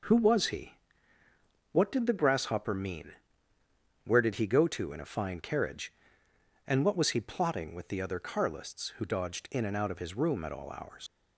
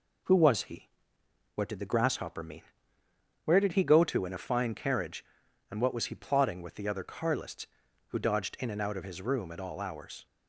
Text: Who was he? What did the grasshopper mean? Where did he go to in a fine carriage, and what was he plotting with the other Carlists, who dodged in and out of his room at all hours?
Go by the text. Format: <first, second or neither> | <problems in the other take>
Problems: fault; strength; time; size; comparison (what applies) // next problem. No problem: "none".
second | leaves "hours" unfinished; at 11.0 s; 75 ms